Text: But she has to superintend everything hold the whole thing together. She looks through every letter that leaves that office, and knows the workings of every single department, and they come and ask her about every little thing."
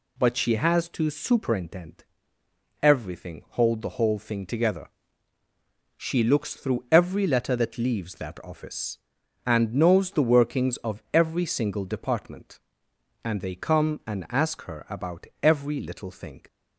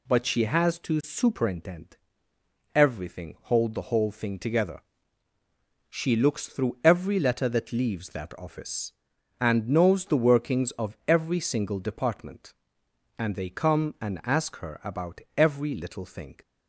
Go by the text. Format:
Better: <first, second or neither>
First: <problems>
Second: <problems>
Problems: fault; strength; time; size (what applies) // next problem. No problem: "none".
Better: neither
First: pauses between "superintend" and "everything"; noticeable; at 2.0 s; 0.78 s long // pauses between "about" and "every"; slight; at 15.2 s; 0.16 s long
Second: pauses between "superintend" and "everything"; noticeable; at 1.9 s; 0.78 s long // pauses between "about" and "every"; slight; at 15.2 s; 0.16 s long